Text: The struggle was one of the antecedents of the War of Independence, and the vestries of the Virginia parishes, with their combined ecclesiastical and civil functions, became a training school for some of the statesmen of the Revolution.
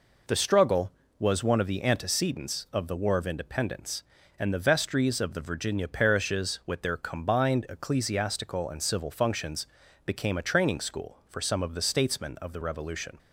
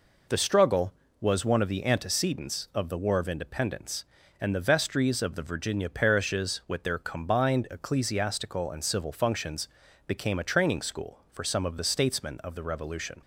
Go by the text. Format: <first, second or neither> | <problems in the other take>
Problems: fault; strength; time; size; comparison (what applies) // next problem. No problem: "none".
neither | none